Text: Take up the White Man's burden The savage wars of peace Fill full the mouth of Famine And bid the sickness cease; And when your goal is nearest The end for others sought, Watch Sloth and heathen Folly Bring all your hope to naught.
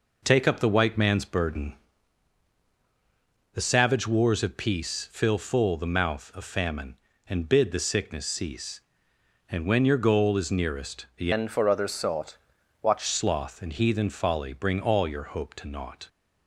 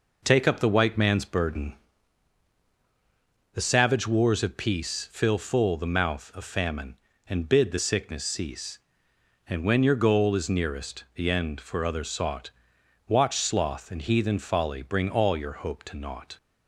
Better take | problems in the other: second | pauses between "burden" and "The"; strong; at 1.7 s; 1.8 s long; strong in the second // changes voice from "end" to "Watch"; from 11.3 to 13.0 s; 1.7 s long

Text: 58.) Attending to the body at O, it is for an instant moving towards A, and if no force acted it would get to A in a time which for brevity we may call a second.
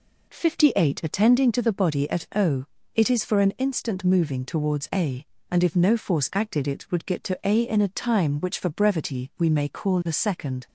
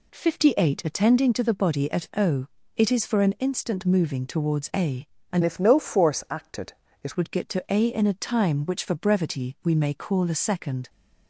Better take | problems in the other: first | changes voice from "if" to "it"; from 5.4 to 7.1 s; 1.7 s long // pauses between "acted" and "it"; slight; at 6.7 s; 0.32 s long

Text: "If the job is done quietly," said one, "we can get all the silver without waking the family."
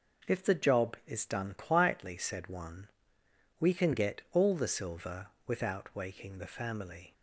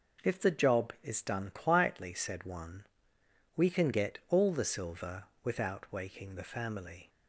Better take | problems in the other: neither | pauses between "silver" and "without"; slight; the same in both

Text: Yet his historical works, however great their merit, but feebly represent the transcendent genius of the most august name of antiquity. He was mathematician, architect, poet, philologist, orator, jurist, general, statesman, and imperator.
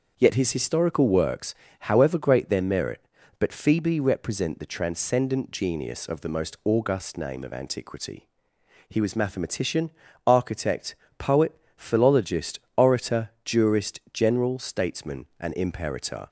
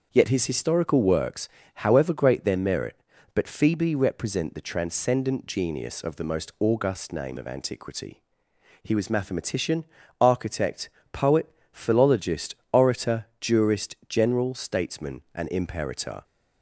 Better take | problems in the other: neither | starts louder than the rest; the same in both

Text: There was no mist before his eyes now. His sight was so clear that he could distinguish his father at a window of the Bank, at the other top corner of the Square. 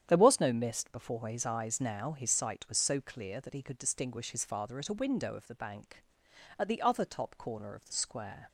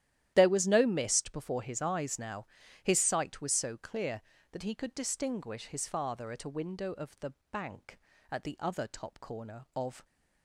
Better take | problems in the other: first | starts louder than the rest; strong; until 1.3 s; 12 dB; strong in the first // pauses between "the" and "Bank"; slight; at 7.3 s; 0.20 s long // stops before "the Square"; at 10.0 s

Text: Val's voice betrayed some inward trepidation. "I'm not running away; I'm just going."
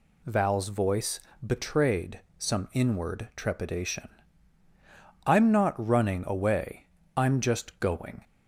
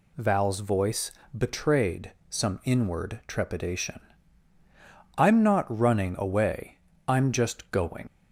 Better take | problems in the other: first | pauses between "voice" and "betrayed"; slight; at 1.0 s; 0.26 s long; slight in the first // pauses between "betrayed" and "some"; slight; at 2.1 s; 0.18 s long; slight in the first // leaves "going" unfinished; at 8.0 s; 75 ms

